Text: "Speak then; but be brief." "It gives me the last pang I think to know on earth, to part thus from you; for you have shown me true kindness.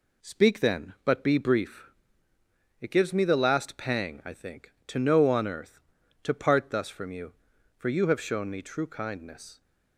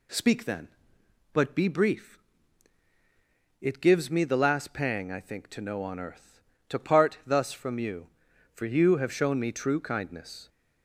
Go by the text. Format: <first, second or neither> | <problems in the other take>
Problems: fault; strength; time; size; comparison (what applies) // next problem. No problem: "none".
neither | none